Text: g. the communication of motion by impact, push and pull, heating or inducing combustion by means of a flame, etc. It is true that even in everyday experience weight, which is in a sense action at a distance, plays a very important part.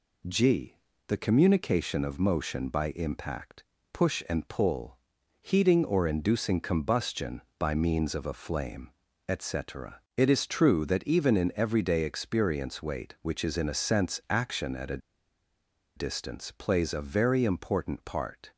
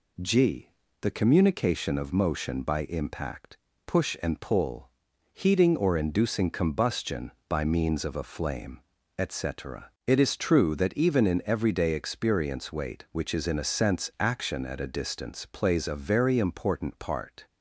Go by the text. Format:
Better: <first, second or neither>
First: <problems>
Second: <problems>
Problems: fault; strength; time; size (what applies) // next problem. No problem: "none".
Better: second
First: pauses between "a" and "distance"; at 14.9 s; 0.98 s long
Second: none